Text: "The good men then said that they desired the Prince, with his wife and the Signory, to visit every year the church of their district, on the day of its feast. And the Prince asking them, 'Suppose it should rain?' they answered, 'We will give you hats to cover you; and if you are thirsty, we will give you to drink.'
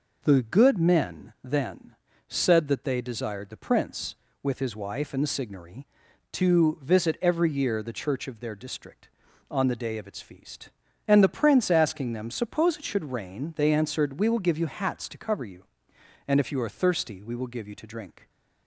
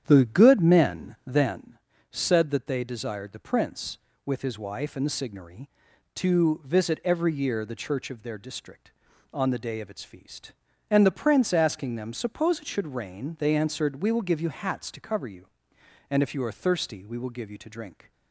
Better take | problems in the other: first | starts louder than the rest; strong; until 1.7 s; 9 dB // pauses between "then" and "said"; slight; at 1.7 s; 0.32 s long; slight in the first

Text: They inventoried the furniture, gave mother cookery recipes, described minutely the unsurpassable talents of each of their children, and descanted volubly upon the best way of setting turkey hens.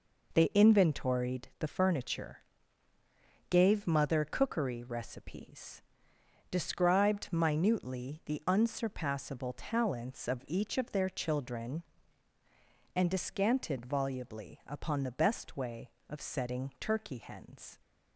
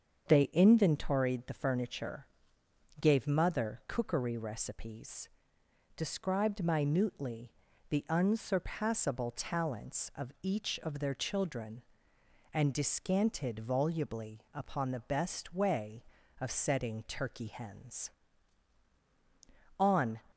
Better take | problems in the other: first | starts louder than the rest; until 1.3 s; 7 dB // pauses between "minutely" and "the"; at 7.5 s; 0.38 s long // goes on to say "On"; slight; from 19.7 s on; 0.42 s long

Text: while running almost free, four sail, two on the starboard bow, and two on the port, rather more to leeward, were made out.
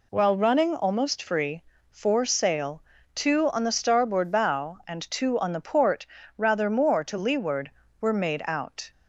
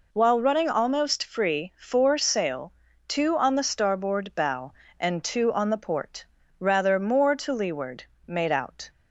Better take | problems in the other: first | skips "were"; at 8.1 s

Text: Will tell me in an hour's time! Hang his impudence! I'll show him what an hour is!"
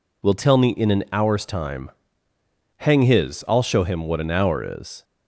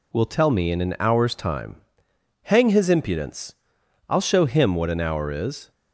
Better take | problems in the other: second | skips "impudence"; at 3.4 s

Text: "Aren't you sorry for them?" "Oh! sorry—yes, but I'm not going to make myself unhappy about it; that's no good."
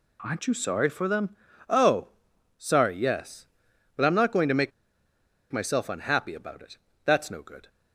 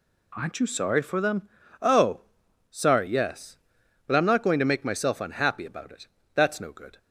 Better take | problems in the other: second | pauses between "make" and "myself"; noticeable; at 4.7 s; 0.79 s long

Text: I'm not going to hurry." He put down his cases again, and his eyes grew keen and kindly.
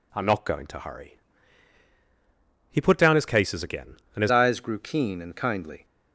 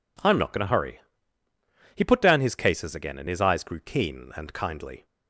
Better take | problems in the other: second | changes voice at "eyes"; from 4.3 s on; 1.5 s long

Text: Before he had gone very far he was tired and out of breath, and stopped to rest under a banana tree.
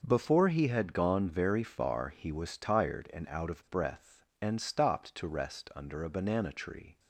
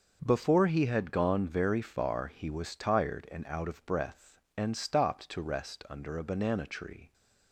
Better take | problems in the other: neither | starts louder than the rest; noticeable; the same in both

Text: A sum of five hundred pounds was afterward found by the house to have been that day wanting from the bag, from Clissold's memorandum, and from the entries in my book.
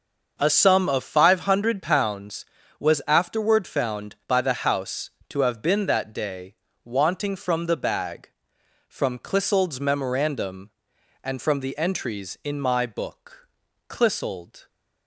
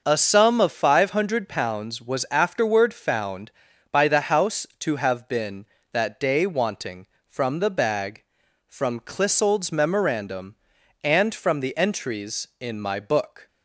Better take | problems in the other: second | starts louder than the rest; noticeable; until 1.4 s; 6 dB; noticeable in the second // pauses between "day" and "wanting"; slight; at 6.5 s; 0.30 s long // goes on to say "Clissold"; noticeable; from 13.8 s on; 0.78 s long

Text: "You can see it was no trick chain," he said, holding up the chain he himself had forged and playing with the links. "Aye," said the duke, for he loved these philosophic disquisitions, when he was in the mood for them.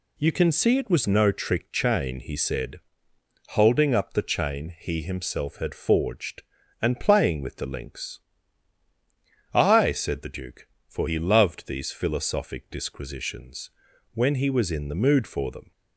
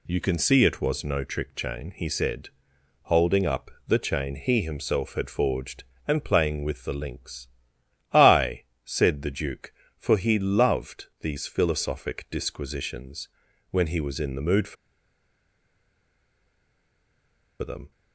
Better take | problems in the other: first | pauses between "up" and "the"; slight; at 3.7 s; 0.16 s long // pauses between "for" and "them"; strong; at 14.7 s; 2.8 s long

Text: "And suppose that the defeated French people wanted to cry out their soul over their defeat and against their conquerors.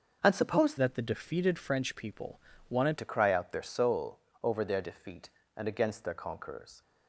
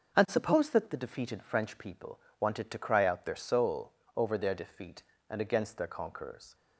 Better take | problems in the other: second | starts louder than the rest; until 1.2 s; 6.5 dB; also in the second // changes voice from "that" to "wanted"; from 0.7 to 2.9 s; 2.2 s long // pauses between "people" and "wanted"; slight; at 2.3 s; 0.30 s long; slight in the second // pauses between "soul" and "over"; slight; at 4.1 s; 0.22 s long; slight in the second

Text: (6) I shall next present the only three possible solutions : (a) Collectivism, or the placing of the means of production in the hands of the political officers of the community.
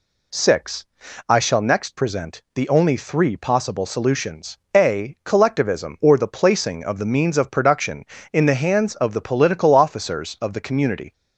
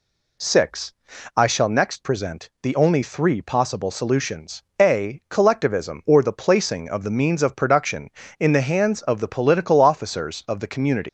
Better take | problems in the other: first | leaves "community" unfinished; at 11.0 s; 100 ms

